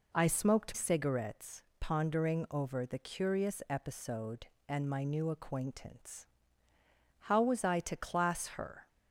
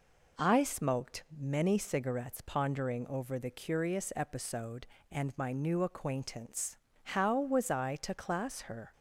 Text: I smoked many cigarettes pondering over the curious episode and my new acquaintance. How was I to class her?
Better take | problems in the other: second | skips "many"; at 0.7 s // pauses between "cigarettes" and "pondering"; slight; at 1.6 s; 0.18 s long

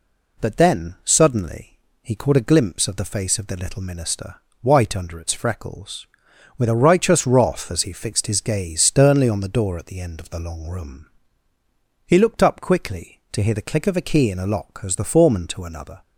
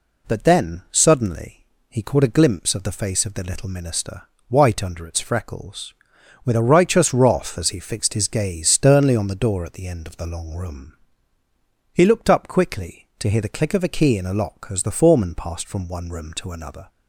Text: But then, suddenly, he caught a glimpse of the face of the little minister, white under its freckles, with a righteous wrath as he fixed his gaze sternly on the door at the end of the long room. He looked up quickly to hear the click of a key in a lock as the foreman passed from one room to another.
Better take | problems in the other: second | skips "passed from one room"; at 15.4 s

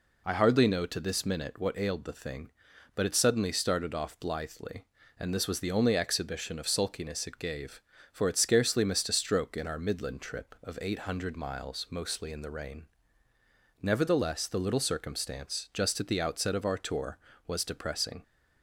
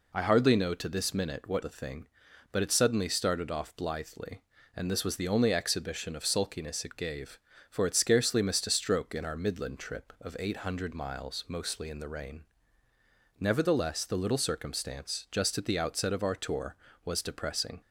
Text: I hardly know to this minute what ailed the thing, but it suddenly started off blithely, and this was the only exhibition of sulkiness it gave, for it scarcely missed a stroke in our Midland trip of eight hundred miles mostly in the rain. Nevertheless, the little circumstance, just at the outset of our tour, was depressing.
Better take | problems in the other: first | skips "ailed"; at 1.6 s

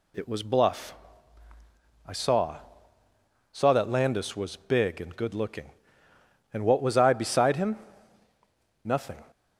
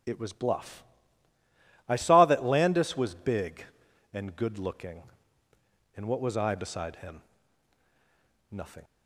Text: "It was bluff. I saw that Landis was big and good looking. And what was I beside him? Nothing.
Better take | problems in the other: second | says "saw" twice; at 3.5 s

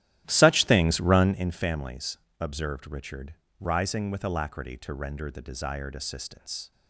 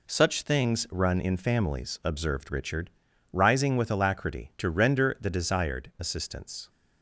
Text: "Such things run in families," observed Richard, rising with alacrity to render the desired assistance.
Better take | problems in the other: second | starts louder than the rest; strong; until 1.5 s; 13.5 dB

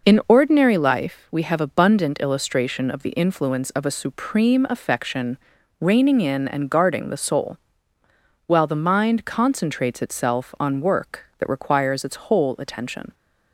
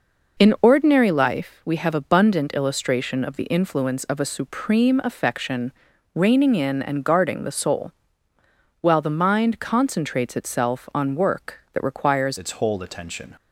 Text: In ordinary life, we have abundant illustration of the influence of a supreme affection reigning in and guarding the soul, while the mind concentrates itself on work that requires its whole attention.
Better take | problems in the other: first | pauses between "affection" and "reigning"; at 5.7 s; 0.42 s long; also in the first // changes voice at "its"; from 12.3 s on; 1.0 s long

